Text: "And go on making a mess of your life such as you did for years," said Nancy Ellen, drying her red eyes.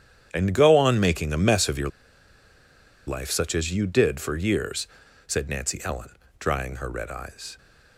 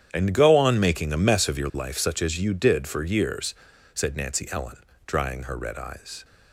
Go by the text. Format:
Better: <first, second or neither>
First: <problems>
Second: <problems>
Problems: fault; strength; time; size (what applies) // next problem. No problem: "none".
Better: second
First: starts louder than the rest; strong; until 1.3 s; 9.5 dB // pauses between "your" and "life"; at 1.8 s; 1.1 s long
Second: starts louder than the rest; strong; until 1.1 s; 9.5 dB